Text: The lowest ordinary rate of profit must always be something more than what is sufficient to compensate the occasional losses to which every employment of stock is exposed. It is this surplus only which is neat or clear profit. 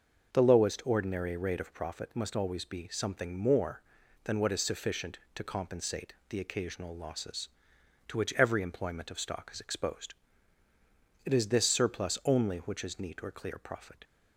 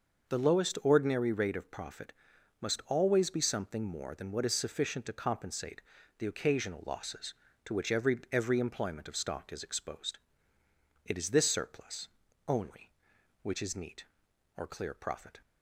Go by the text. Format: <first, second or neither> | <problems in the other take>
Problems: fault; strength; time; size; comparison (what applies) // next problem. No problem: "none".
first | pauses between "profit" and "must"; noticeable; at 2.1 s; 0.48 s long // pauses between "compensate" and "the"; slight; at 5.8 s; 0.34 s long; slight in the first // says "every" twice; at 8.3 s // pauses between "surplus" and "only"; at 12.0 s; 0.38 s long